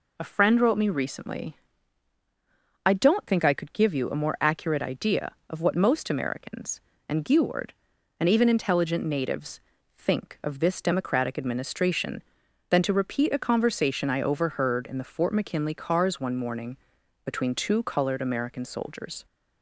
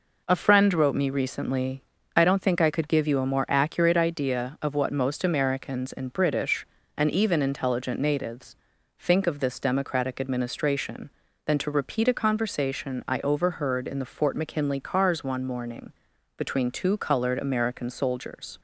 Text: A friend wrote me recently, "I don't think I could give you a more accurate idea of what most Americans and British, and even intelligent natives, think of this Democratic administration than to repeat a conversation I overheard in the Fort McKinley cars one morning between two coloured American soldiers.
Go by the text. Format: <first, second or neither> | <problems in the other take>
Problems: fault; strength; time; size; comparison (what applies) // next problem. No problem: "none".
second | says "Geward" for "British"; at 7.2 s // pauses between "morning" and "between"; noticeable; at 16.7 s; 0.48 s long; noticeable in the second